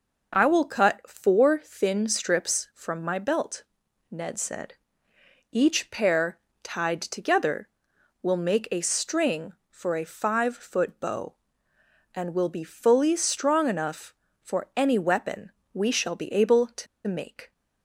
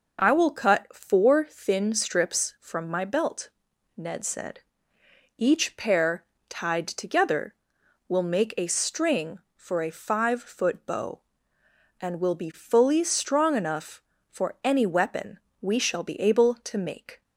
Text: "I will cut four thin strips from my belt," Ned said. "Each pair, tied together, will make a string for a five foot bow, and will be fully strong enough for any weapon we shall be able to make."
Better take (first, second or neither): second